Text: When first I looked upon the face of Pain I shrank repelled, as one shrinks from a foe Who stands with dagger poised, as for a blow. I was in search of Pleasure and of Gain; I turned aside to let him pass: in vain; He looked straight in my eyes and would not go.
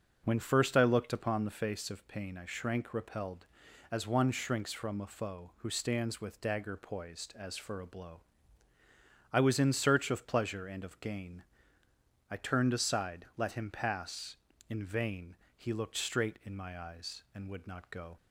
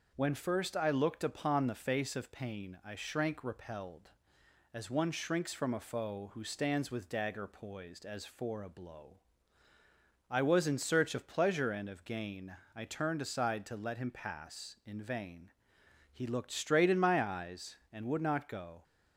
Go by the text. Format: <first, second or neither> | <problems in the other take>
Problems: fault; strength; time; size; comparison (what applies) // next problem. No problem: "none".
second | skips "to"; at 13.3 s